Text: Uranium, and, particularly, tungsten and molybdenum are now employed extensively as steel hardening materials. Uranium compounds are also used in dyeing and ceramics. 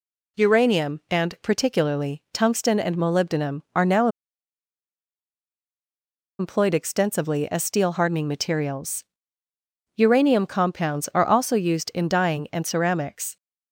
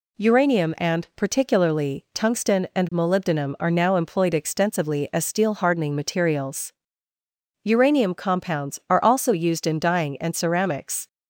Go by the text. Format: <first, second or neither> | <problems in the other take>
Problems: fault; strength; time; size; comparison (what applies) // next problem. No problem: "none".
second | pauses between "now" and "employed"; strong; at 4.0 s; 2.3 s long